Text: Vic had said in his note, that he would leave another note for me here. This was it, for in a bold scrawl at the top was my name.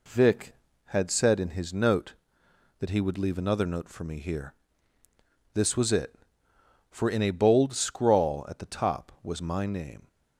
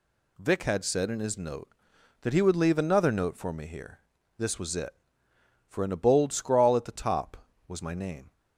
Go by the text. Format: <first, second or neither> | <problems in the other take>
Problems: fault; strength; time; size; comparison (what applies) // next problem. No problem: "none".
neither | none